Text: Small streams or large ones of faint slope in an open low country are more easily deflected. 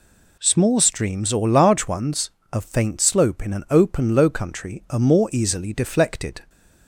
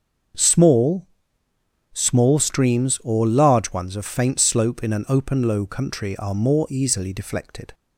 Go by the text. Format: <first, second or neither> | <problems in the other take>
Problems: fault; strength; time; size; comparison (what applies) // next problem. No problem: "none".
first | starts louder than the rest; until 2.2 s; 6.5 dB // says "Small" twice; at 1.9 s